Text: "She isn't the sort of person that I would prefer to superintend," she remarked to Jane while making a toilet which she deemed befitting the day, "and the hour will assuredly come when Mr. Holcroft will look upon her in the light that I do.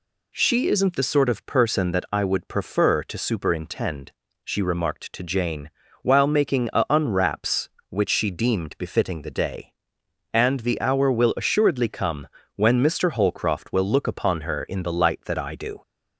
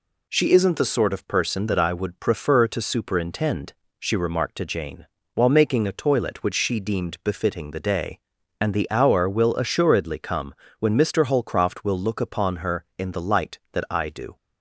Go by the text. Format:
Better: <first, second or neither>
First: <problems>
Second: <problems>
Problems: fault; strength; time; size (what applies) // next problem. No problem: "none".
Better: second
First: pauses between "Jane" and "while"; slight; at 5.6 s; 0.32 s long // says "unwraps" for "toilet"; at 6.8 s // pauses between "come" and "when"; slight; at 12.2 s; 0.30 s long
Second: pauses between "Jane" and "while"; slight; at 5.0 s; 0.30 s long // pauses between "come" and "when"; slight; at 10.5 s; 0.24 s long